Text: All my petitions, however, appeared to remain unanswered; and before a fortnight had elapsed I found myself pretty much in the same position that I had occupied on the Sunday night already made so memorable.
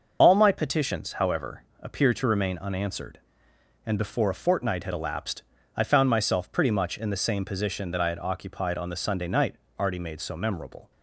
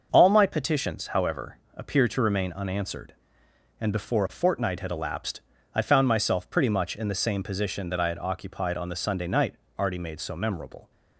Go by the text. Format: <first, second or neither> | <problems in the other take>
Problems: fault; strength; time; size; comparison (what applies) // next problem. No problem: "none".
second | loses the start of "All"; at 0.2 s; 30 ms // starts louder than the rest; noticeable; until 1.2 s; 6 dB; also in the second // pauses between "elapsed" and "I"; slight; at 5.4 s; 0.34 s long; slight in the second // pauses between "night" and "already"; slight; at 9.5 s; 0.24 s long; slight in the second